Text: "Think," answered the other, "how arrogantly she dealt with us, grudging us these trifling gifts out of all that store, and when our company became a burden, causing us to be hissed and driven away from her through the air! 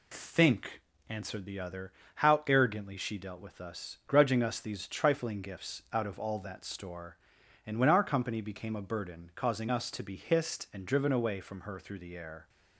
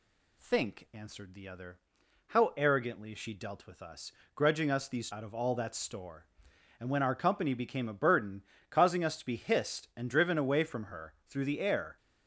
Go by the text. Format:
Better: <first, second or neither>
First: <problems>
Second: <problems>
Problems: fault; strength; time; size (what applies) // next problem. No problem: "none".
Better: first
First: none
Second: skips "trifling gifts"; at 5.0 s